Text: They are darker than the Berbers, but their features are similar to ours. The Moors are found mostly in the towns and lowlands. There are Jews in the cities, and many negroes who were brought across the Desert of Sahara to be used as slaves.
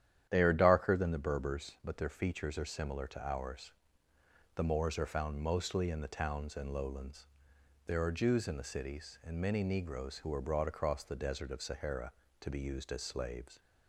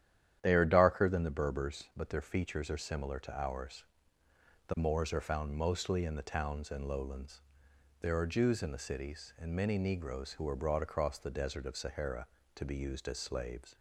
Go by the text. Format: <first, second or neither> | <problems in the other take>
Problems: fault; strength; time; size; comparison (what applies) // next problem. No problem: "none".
neither | starts louder than the rest; strong; the same in both